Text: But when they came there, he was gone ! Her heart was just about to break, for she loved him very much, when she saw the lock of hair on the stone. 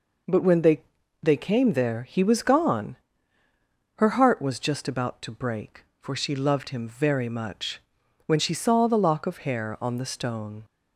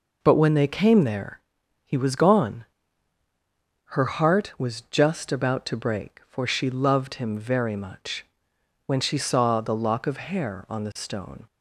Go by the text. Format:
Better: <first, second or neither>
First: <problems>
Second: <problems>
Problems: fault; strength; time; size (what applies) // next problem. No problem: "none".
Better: second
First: says "they" twice; at 1.2 s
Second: none